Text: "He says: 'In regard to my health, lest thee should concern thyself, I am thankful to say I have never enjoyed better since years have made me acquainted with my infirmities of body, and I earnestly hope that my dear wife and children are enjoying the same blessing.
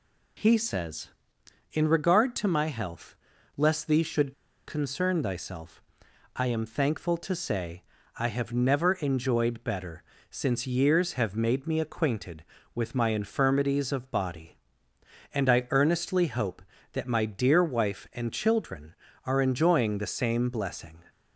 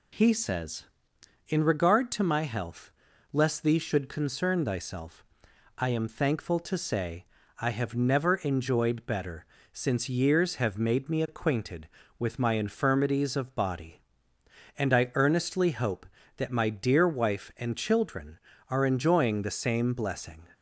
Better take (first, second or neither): second